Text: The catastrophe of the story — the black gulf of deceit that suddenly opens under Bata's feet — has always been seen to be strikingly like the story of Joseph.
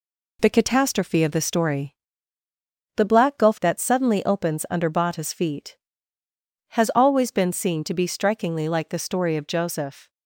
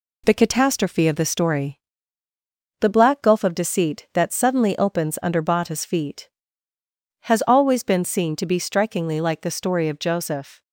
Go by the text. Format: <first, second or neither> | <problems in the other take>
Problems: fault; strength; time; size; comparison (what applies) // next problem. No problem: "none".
second | skips "of deceit"; at 3.6 s